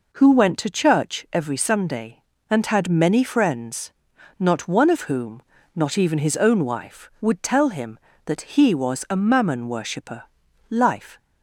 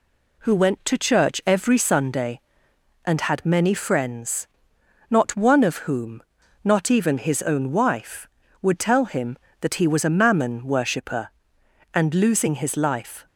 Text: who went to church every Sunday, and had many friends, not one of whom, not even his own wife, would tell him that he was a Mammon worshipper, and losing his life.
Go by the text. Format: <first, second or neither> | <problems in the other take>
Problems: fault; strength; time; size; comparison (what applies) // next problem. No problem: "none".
second | skips "and losing his"; at 10.4 s